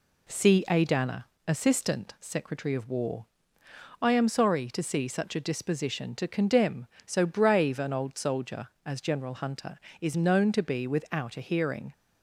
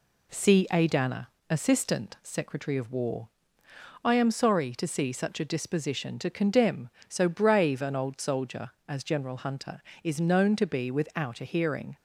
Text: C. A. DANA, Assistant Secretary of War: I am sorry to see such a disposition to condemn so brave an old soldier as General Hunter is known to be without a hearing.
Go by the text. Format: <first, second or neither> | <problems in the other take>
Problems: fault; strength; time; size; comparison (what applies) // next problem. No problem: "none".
neither | none